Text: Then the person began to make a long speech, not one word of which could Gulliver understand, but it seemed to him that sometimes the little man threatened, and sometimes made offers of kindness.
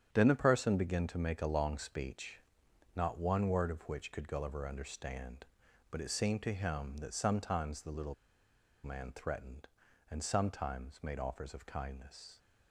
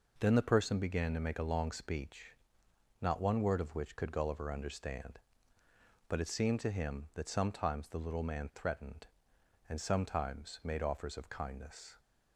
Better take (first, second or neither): second